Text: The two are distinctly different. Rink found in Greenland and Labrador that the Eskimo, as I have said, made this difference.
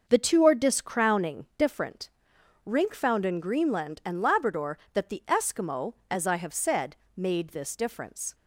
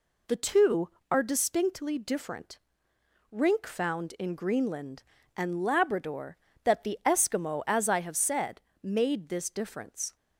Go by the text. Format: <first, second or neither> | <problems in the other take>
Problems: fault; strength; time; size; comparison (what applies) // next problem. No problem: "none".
second | starts louder than the rest; until 1.0 s; 6.5 dB // says "discrowning" for "distinctly"; at 0.5 s